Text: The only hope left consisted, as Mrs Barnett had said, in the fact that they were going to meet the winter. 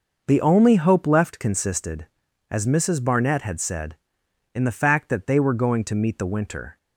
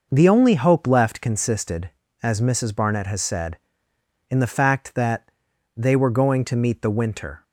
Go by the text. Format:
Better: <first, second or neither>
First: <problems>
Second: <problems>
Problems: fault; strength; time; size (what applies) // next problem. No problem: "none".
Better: first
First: none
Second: says "has" for "had"; at 3.0 s // pauses between "that" and "they"; noticeable; at 5.3 s; 0.46 s long